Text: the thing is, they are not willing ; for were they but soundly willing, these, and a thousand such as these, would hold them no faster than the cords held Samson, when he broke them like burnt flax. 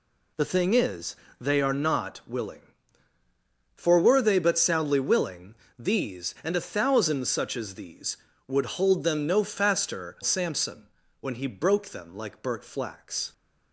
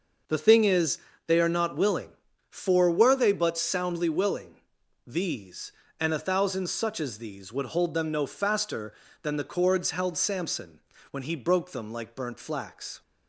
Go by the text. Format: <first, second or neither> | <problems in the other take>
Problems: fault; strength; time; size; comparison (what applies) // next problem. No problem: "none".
second | skips "than the cords held"; at 10.2 s